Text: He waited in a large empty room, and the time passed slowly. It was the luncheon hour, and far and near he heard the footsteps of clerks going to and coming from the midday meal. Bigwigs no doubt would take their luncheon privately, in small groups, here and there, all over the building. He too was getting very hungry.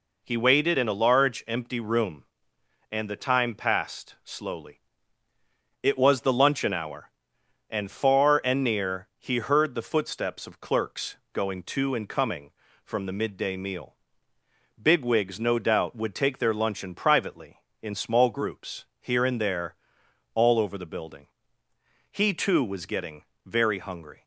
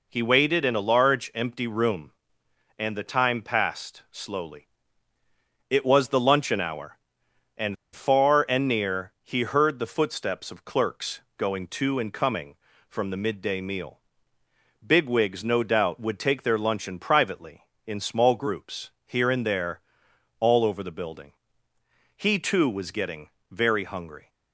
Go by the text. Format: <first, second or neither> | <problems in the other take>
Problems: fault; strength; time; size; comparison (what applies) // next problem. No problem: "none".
first | pauses between "and" and "far"; slight; at 7.7 s; 0.18 s long // pauses between "clerks" and "going"; slight; at 11.2 s; 0.16 s long; slight in the first // pauses between "getting" and "very"; slight; at 23.2 s; 0.22 s long; slight in the first